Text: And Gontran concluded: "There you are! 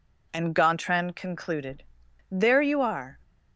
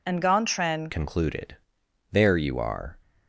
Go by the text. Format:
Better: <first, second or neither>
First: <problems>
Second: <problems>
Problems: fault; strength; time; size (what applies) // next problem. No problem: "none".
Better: first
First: none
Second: changes voice at "concluded"; from 0.8 s on; 2.1 s long